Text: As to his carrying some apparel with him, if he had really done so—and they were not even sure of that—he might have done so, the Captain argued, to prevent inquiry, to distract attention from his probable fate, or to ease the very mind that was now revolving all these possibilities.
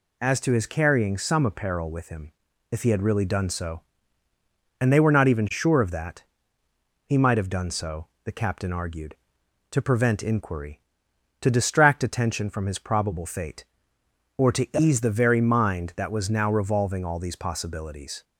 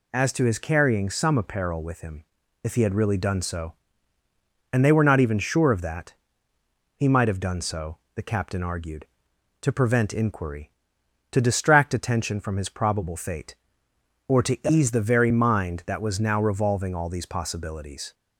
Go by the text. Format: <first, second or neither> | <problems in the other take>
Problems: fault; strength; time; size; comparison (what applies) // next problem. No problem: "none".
neither | none